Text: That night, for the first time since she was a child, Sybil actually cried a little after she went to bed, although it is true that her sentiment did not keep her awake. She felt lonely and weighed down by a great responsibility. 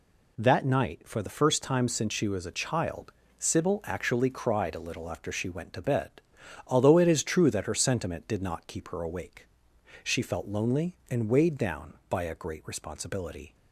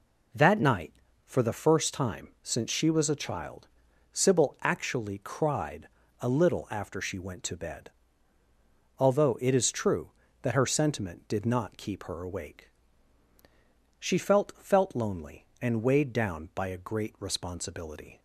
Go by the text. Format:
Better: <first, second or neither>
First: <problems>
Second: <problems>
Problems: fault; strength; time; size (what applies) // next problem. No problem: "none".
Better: first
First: none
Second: pauses between "cried" and "a"; slight; at 5.8 s; 0.34 s long // says "felt" twice; at 14.5 s